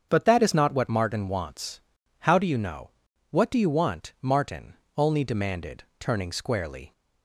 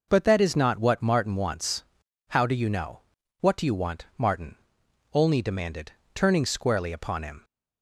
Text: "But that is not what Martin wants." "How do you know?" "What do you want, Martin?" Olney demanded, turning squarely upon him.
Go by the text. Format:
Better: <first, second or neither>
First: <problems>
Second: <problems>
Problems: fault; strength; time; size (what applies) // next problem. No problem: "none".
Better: second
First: starts louder than the rest; strong; until 1.1 s; 7.5 dB // stops before "upon him"; at 6.9 s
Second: none